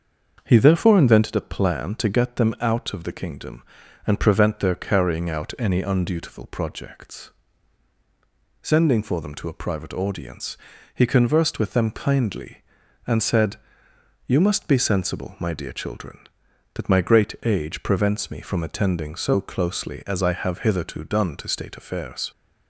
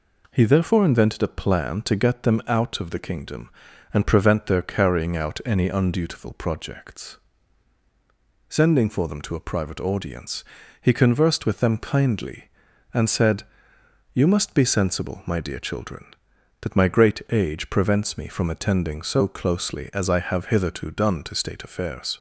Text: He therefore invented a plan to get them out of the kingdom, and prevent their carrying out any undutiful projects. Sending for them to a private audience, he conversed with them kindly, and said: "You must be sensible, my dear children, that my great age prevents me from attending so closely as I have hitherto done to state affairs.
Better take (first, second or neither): second